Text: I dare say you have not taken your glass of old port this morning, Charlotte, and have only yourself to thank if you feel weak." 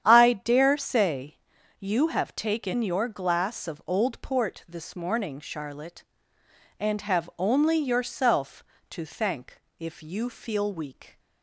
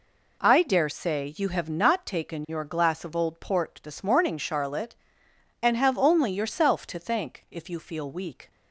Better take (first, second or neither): second